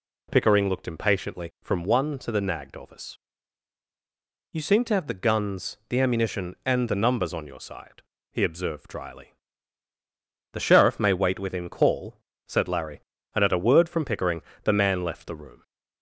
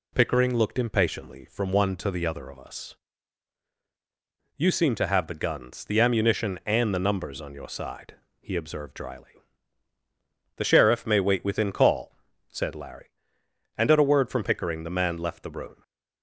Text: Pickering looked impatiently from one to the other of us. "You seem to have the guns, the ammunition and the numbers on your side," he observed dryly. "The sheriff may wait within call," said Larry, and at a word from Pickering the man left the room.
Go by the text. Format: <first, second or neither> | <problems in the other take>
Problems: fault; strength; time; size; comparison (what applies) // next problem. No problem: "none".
second | says "nagged" for "other"; at 2.4 s // pauses between "Pickering" and "the"; slight; at 14.4 s; 0.22 s long